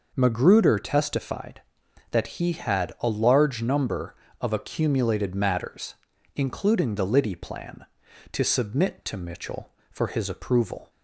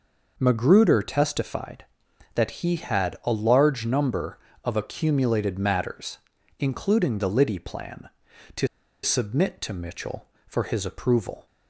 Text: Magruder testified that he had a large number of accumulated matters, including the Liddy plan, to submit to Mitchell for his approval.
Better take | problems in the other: first | pauses between "to" and "submit"; at 8.6 s; 0.36 s long

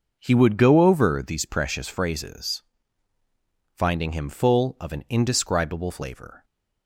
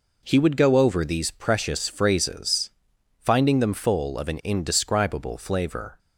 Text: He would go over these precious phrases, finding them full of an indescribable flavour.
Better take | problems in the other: second | says "him" for "them"; at 4.1 s

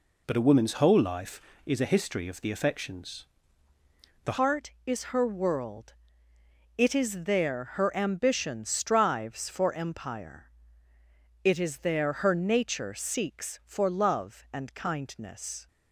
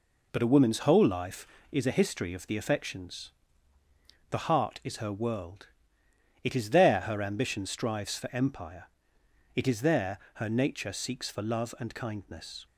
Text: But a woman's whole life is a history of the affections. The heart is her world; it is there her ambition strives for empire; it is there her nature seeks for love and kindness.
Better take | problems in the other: second | changes voice at "heart"; from 4.3 s on; 11.3 s long

